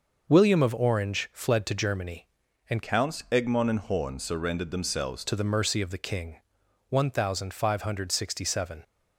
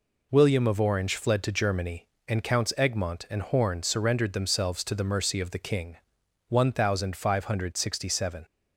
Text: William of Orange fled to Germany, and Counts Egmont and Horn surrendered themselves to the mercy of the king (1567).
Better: second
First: changes voice from "Counts" to "themselves"; from 2.8 to 5.2 s; 2.4 s long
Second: none

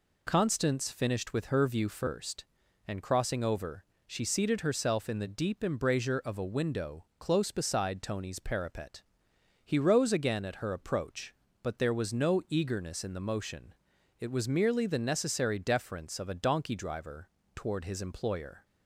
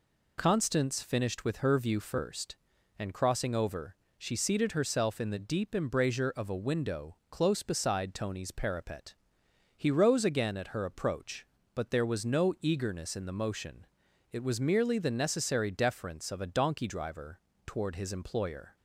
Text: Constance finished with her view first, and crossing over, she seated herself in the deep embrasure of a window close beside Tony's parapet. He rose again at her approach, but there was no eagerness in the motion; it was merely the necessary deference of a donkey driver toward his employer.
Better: neither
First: pauses between "driver" and "toward"; slight; at 17.2 s; 0.26 s long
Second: pauses between "driver" and "toward"; slight; at 17.4 s; 0.26 s long

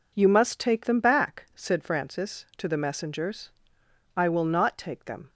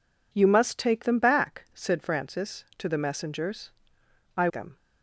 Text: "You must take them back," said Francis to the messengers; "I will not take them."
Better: first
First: none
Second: skips "will not take"; at 4.4 s

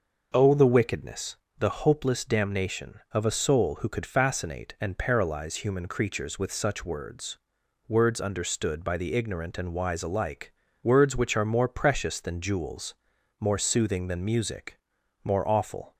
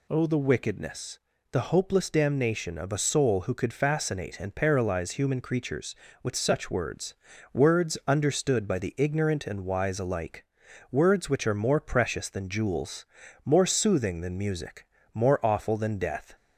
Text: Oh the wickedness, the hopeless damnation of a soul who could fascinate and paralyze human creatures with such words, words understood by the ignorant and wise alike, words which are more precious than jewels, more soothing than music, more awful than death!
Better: second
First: stops before "than death"; at 15.9 s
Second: none

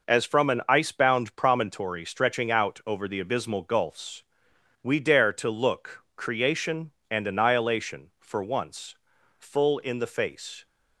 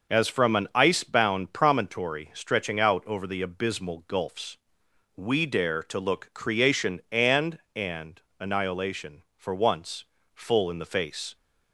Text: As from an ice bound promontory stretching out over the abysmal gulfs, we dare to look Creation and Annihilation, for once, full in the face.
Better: first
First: none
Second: says "and" twice; at 7.7 s

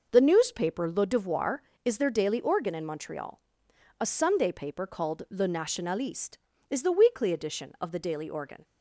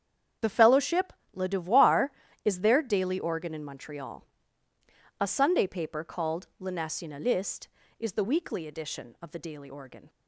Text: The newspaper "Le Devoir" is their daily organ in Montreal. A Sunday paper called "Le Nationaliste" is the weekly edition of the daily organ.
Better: first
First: none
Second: starts louder than the rest; strong; until 1.6 s; 8 dB // says "fellowship" for "newspaper"; at 0.4 s

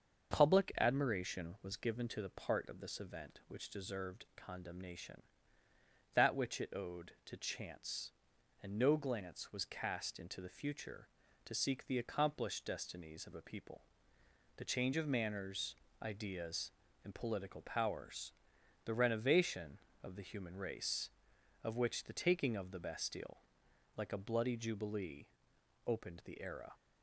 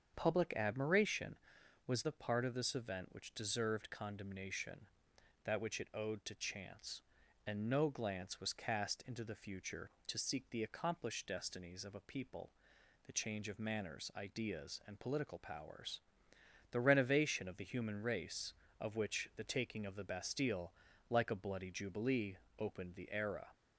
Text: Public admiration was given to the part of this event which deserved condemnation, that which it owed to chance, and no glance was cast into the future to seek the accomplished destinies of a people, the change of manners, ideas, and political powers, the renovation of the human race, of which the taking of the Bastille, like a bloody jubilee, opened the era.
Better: first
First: starts louder than the rest; until 1.3 s; 6.5 dB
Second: starts louder than the rest; strong; until 1.1 s; 7.5 dB // skips "given to"; at 2.0 s

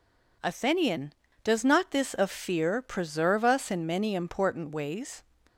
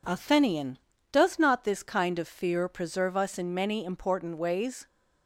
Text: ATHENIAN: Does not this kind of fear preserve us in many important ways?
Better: second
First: skips "kind"; at 2.1 s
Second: none

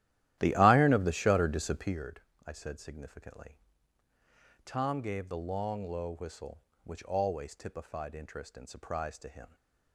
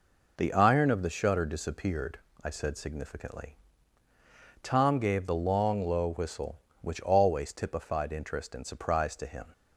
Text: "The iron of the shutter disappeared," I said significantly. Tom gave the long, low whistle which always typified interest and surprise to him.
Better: second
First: starts louder than the rest; strong; until 2.1 s; 13 dB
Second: none

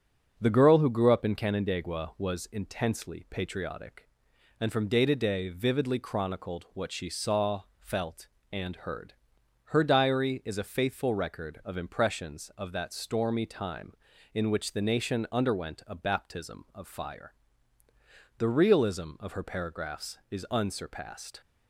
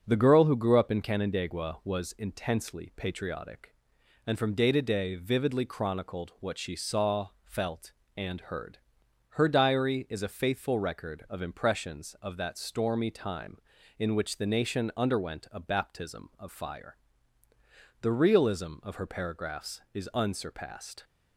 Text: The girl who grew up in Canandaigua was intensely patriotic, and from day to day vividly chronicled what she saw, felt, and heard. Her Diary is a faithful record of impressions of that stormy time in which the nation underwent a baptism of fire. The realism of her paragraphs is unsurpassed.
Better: neither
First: starts louder than the rest; until 1.3 s; 6.5 dB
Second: starts louder than the rest; until 1.0 s; 6.5 dB

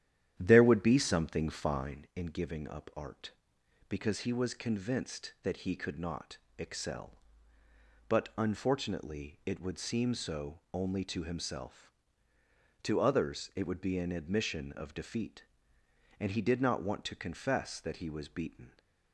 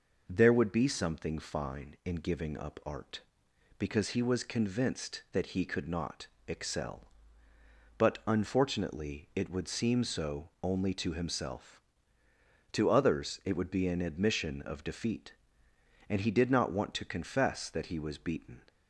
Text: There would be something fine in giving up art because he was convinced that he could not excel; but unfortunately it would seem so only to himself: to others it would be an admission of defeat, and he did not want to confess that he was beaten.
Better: second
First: starts louder than the rest; strong; until 2.2 s; 10.5 dB // pauses between "not" and "excel"; slight; at 6.3 s; 0.22 s long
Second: pauses between "not" and "excel"; slight; at 6.2 s; 0.22 s long

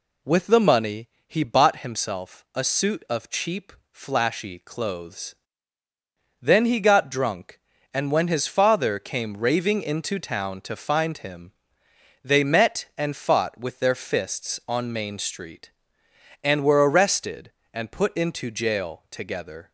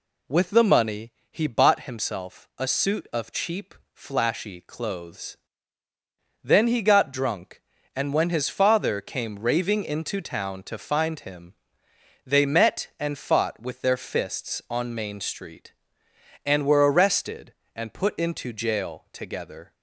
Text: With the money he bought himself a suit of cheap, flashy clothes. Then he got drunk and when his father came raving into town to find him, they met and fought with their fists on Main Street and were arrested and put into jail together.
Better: neither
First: pauses between "money" and "he"; slight; at 1.0 s; 0.18 s long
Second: pauses between "money" and "he"; slight; at 1.1 s; 0.18 s long

